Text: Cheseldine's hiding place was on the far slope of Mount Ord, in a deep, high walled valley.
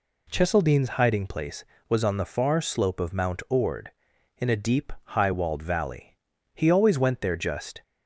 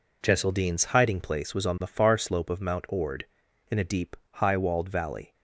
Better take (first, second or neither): second